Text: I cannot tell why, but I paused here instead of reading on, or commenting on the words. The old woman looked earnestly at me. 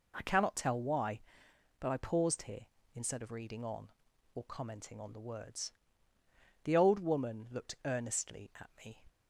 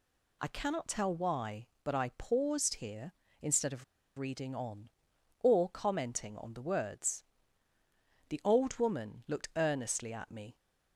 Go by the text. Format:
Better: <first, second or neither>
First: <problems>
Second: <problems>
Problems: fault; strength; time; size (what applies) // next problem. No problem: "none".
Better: first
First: none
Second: pauses between "of" and "reading"; slight; at 3.8 s; 0.34 s long